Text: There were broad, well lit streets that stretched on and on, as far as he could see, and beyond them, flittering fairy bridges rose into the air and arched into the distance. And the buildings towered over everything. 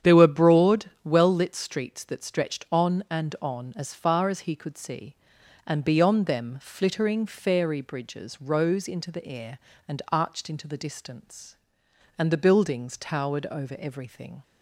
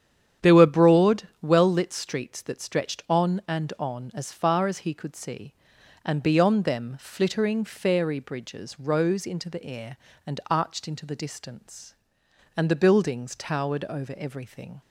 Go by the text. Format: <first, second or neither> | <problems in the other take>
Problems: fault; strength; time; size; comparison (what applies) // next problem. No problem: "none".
neither | starts louder than the rest; strong; the same in both